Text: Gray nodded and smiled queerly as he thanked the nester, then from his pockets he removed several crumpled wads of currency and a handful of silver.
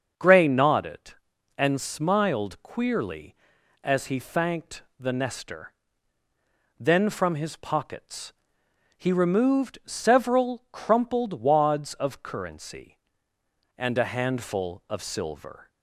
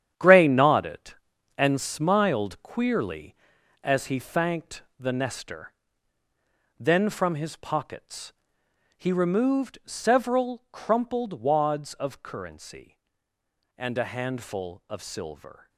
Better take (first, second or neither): first